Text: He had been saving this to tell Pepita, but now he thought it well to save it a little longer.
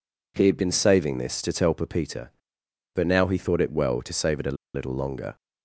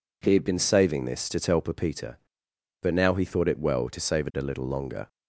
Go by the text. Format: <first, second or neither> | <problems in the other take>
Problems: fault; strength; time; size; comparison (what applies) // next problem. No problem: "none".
second | pauses between "a" and "little"; slight; at 4.5 s; 0.19 s long